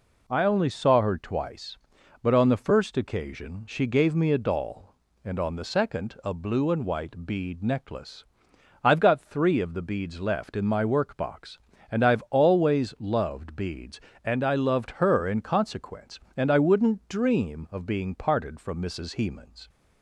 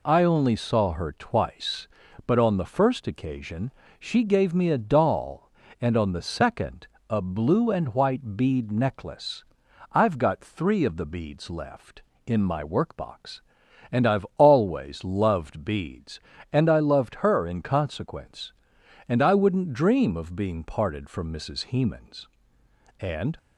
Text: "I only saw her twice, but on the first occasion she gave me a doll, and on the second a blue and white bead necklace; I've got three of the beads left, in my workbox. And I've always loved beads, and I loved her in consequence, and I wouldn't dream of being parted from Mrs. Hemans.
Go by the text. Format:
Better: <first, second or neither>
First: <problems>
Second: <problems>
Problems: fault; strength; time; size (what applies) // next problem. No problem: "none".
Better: first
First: none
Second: pauses between "occasion" and "she"; slight; at 3.7 s; 0.28 s long // pauses between "second" and "a"; slight; at 6.8 s; 0.20 s long // goes on to say "And"; slight; from 22.9 s on; 0.38 s long